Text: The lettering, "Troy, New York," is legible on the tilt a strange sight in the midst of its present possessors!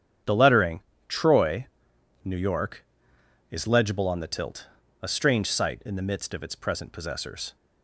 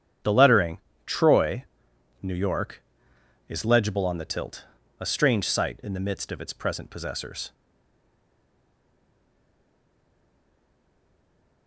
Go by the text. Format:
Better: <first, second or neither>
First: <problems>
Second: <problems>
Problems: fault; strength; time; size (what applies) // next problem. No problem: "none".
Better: first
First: starts louder than the rest; strong; until 1.5 s; 9 dB // pauses between "tilt" and "a"; slight; at 4.6 s; 0.34 s long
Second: starts louder than the rest; strong; until 1.4 s; 9 dB // pauses between "tilt" and "a"; slight; at 4.6 s; 0.34 s long // stays silent after the last word; strong; from 7.5 s on; 4.1 s long